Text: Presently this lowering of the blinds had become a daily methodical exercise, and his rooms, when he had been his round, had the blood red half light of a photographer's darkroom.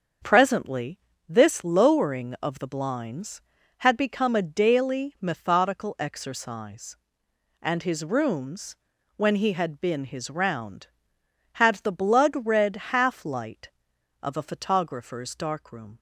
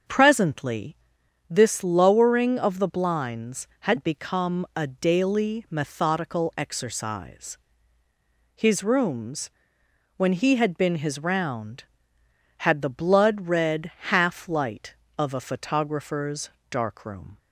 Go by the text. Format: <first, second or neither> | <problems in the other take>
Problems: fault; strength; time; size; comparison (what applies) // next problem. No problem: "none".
first | starts louder than the rest; until 1.6 s; 7 dB; also in the first // pauses between "Presently" and "this"; noticeable; at 0.9 s; 0.54 s long; slight in the first // skips "and"; at 8.0 s // pauses between "red" and "half"; slight; at 13.9 s; 0.16 s long // pauses between "photographer's" and "darkroom"; slight; at 16.4 s; 0.20 s long